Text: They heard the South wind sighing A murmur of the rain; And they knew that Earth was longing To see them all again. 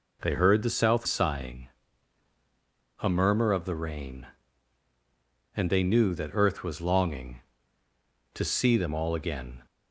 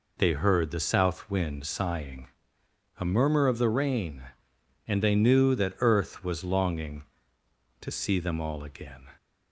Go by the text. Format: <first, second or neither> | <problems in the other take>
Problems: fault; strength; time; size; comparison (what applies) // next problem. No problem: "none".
second | skips "wind"; at 1.0 s // pauses between "sighing" and "A"; strong; at 1.6 s; 1.3 s long; noticeable in the second